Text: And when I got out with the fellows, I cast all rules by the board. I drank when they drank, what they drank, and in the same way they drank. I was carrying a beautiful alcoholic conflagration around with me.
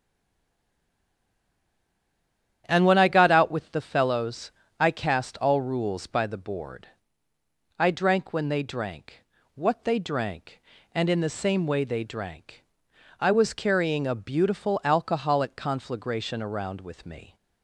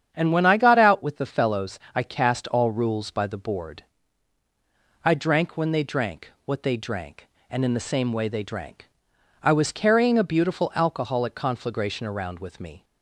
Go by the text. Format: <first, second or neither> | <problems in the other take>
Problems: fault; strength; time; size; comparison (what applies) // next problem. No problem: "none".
second | stays silent before the first word; strong; until 2.6 s; 2.6 s long // starts louder than the rest; strong; until 3.6 s; 10 dB; strong in the second